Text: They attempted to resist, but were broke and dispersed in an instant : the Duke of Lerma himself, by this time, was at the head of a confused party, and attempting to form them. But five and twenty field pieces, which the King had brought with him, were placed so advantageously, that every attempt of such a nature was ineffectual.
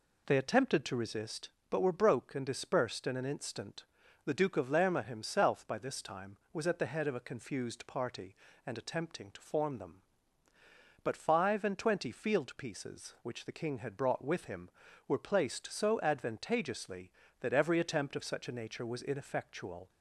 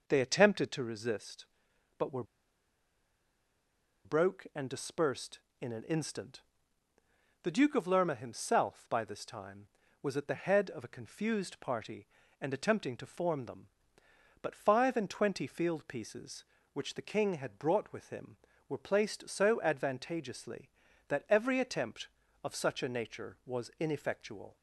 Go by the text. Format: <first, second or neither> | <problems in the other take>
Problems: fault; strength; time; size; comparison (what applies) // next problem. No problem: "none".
first | pauses between "were" and "broke"; strong; at 2.2 s; 1.8 s long